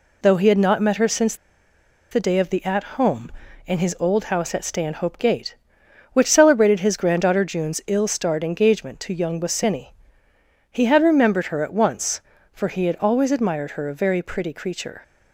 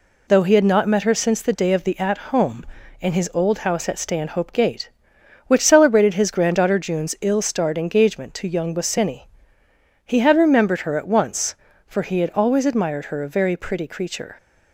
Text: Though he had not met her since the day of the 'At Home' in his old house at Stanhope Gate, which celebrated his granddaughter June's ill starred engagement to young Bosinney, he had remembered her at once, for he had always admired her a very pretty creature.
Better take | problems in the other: second | pauses between "since" and "the"; noticeable; at 1.3 s; 0.76 s long // pauses between "At" and "Home"; slight; at 2.8 s; 0.16 s long; slight in the second

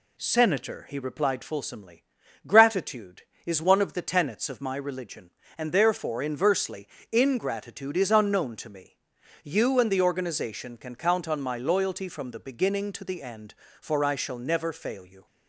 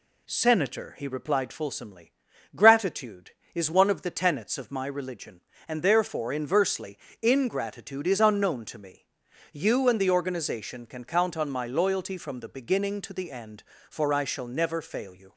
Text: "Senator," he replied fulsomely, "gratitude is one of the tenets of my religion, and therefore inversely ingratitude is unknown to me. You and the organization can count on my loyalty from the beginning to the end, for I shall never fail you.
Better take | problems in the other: neither | pauses between "inversely" and "ingratitude"; slight; the same in both

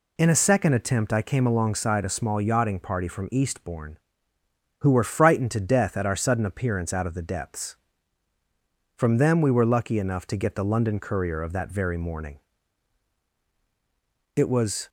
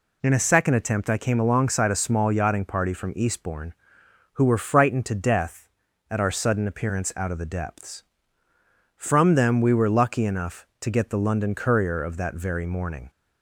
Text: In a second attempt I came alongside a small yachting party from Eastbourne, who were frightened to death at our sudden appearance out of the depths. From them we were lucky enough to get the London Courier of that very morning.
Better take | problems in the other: second | goes on to say "It was"; from 14.3 s on; 0.52 s long

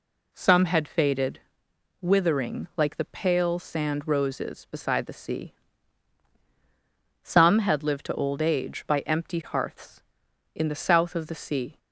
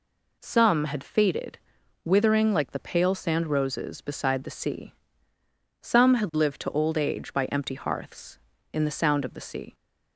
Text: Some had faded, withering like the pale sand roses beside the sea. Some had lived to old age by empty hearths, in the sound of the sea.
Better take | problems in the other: second | says "south" for "sound"; at 10.7 s

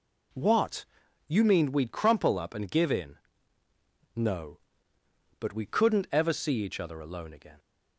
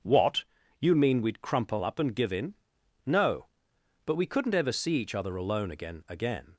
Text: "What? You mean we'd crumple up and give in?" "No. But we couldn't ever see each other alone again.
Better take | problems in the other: first | starts louder than the rest; until 1.3 s; 6.5 dB // says "again" twice; at 6.0 s

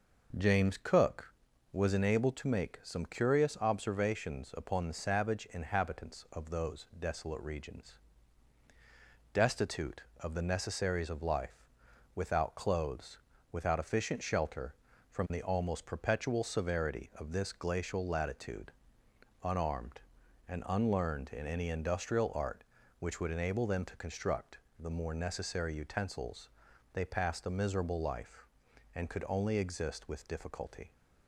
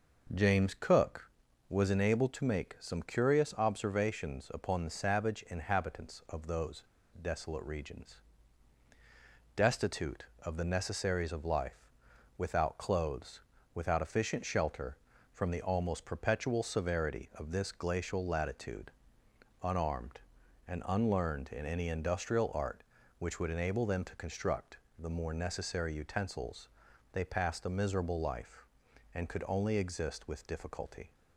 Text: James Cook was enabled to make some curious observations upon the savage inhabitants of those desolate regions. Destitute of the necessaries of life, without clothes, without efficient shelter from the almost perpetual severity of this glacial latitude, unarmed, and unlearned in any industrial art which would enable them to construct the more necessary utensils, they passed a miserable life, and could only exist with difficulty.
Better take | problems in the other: first | pauses between "those" and "desolate"; at 6.8 s; 0.37 s long // pauses between "construct" and "the"; slight; at 24.7 s; 0.22 s long; slight in the first

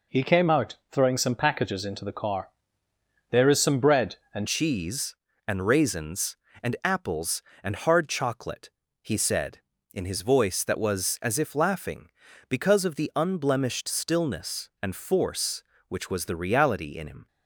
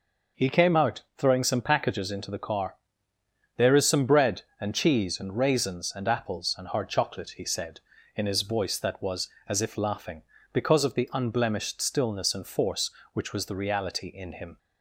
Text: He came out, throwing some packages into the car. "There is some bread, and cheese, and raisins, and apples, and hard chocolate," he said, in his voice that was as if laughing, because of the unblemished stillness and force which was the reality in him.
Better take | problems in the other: second | changes voice at "cheese"; from 4.4 s on; 12.8 s long

